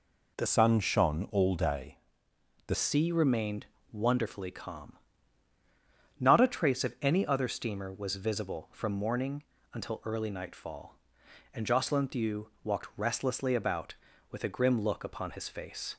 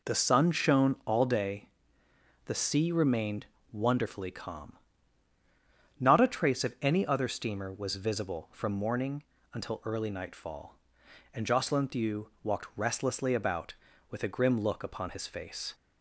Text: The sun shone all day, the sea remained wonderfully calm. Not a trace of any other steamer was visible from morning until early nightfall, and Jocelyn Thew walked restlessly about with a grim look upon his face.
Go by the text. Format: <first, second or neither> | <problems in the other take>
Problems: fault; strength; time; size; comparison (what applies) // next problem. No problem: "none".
second | changes voice from "sun" to "the"; from 0.4 to 2.7 s; 2.3 s long // pauses between "remained" and "wonderfully"; slight; at 3.6 s; 0.24 s long; slight in the second // pauses between "morning" and "until"; slight; at 9.4 s; 0.32 s long; slight in the second